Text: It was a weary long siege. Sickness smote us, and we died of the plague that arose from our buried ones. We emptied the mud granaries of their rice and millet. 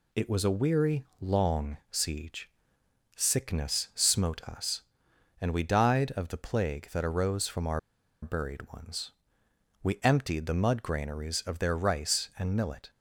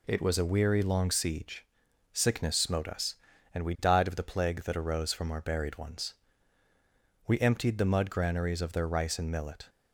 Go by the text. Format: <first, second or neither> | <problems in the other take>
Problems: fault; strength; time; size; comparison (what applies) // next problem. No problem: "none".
second | pauses between "weary" and "long"; slight; at 1.0 s; 0.16 s long // pauses between "our" and "buried"; at 7.7 s; 0.43 s long